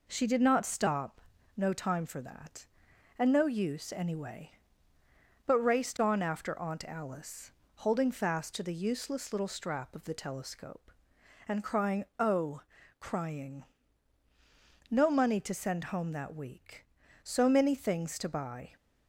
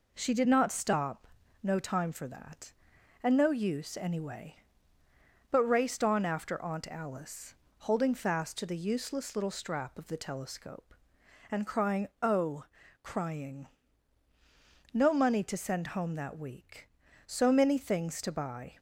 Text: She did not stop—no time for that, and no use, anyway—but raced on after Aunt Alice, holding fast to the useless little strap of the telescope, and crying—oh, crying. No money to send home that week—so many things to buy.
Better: neither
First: none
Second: none

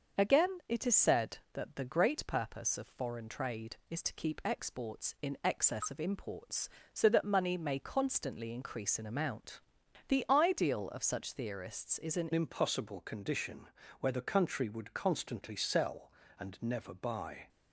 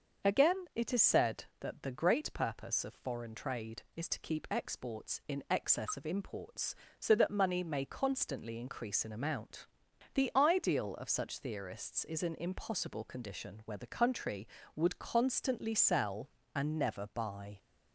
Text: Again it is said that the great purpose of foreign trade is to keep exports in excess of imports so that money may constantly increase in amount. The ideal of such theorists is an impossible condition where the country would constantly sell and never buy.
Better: second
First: starts louder than the rest; until 1.2 s; 6.5 dB // changes voice at "impossible"; from 12.3 s on; 5.1 s long // pauses between "condition" and "where"; slight; at 13.6 s; 0.32 s long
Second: starts louder than the rest; until 1.3 s; 6.5 dB

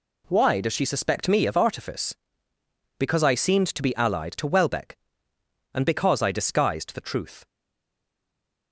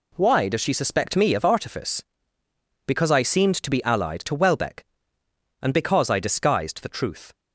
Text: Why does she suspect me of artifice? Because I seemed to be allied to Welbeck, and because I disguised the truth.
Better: second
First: stays silent after the last word; noticeable; from 7.4 s on; 1.3 s long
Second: none

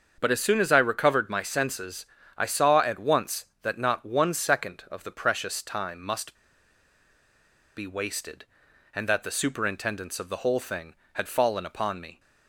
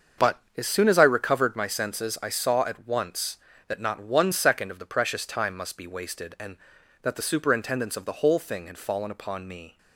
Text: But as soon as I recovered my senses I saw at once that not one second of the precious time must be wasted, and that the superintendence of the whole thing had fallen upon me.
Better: second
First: starts louder than the rest; until 1.1 s; 6.5 dB // pauses between "senses" and "I"; slight; at 2.0 s; 0.32 s long // pauses between "must" and "be"; strong; at 6.3 s; 1.4 s long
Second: starts louder than the rest; until 1.3 s; 7 dB

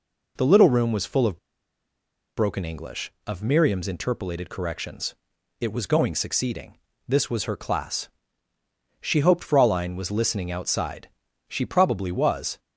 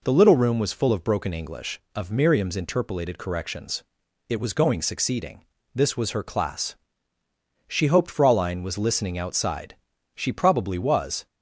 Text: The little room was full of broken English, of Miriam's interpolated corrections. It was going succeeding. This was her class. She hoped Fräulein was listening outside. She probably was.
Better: second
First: pauses between "of" and "broken"; at 1.3 s; 0.99 s long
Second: none

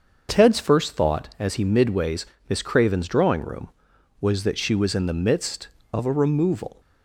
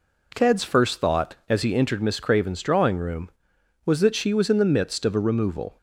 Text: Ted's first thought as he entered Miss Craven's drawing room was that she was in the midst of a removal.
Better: second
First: starts louder than the rest; until 1.4 s; 6.5 dB // says "midways" for "entered"; at 1.6 s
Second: none

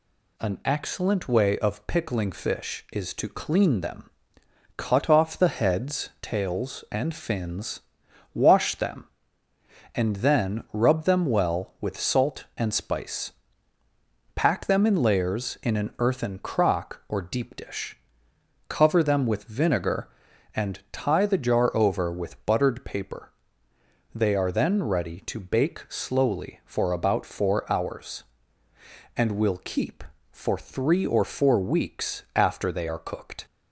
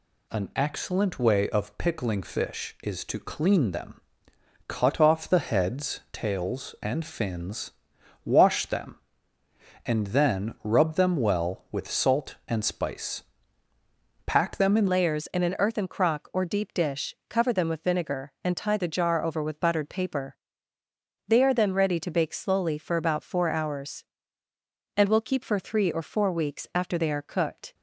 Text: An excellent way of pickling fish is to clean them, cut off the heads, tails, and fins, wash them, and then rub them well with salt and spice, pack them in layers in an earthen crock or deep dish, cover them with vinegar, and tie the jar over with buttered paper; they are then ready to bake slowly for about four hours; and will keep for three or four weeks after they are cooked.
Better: first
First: none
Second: changes voice at "layers"; from 14.8 s on; 12.9 s long

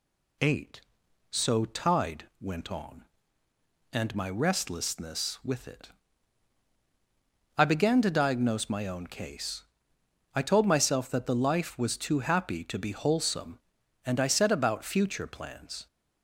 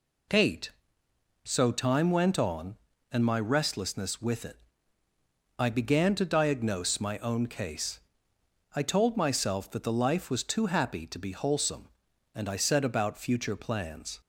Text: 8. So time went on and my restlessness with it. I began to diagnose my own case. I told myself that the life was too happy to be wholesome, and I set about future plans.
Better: second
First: says "tide" for "time"; at 1.6 s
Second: none

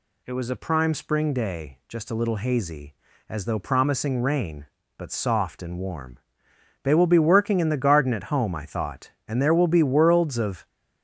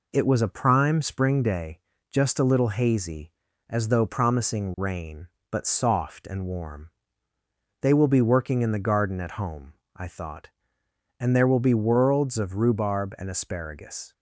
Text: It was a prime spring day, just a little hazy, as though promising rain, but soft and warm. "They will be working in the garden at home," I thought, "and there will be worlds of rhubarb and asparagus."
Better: second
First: stops before "rhubarb and asparagus"; at 10.6 s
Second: none

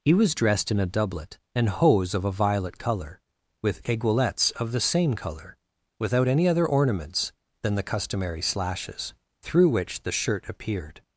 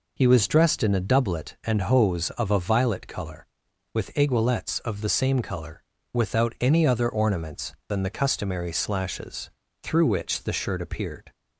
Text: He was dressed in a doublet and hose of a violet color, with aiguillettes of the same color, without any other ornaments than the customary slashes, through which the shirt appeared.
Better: neither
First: none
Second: none

